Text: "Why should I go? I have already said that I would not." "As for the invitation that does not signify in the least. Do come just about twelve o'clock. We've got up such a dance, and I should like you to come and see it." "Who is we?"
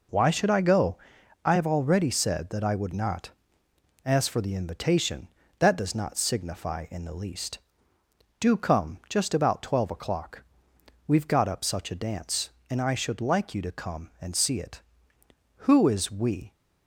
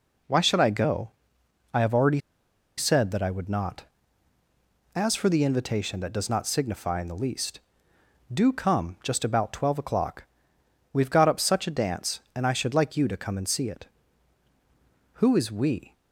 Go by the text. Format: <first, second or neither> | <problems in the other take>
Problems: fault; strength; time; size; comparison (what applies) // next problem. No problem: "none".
first | pauses between "already" and "said"; noticeable; at 2.1 s; 0.57 s long